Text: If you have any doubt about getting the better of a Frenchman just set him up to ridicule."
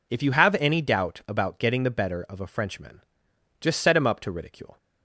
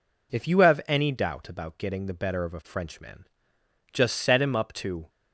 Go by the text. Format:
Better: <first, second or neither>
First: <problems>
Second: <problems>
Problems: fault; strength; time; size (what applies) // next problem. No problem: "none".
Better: first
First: pauses between "Frenchman" and "just"; noticeable; at 3.0 s; 0.60 s long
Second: pauses between "Frenchman" and "just"; noticeable; at 3.2 s; 0.66 s long // stops before "ridicule"; at 5.0 s